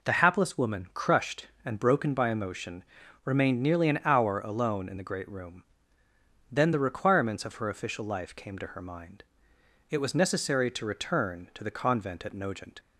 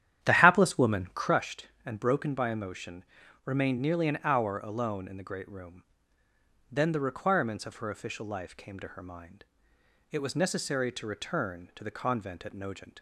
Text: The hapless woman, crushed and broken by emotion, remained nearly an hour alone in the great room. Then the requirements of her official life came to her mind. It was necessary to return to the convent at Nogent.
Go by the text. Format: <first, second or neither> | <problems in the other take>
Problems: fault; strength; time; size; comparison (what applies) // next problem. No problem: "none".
first | starts louder than the rest; strong; until 1.4 s; 11 dB